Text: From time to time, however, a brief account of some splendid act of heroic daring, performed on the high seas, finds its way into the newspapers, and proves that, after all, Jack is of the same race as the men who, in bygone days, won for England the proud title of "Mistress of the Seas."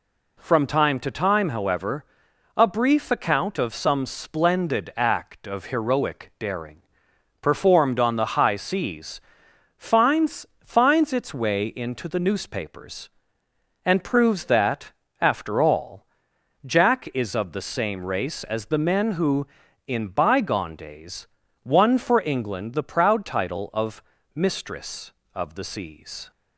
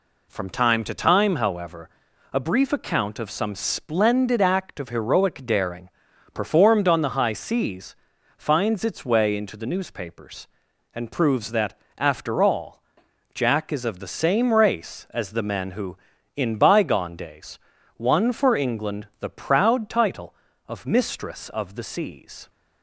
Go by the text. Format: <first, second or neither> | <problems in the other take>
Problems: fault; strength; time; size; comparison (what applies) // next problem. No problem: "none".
second | says "finds" twice; at 10.6 s // pauses between "of" and "Mistress"; slight; at 24.0 s; 0.32 s long